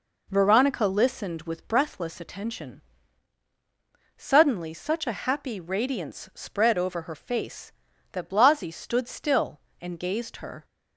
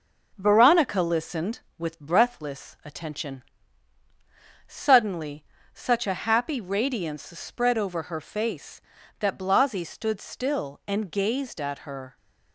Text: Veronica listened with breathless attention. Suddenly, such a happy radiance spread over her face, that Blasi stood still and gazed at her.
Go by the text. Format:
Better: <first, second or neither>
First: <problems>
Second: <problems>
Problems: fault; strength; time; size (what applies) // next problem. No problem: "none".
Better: second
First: skips "at"; at 10.3 s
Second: none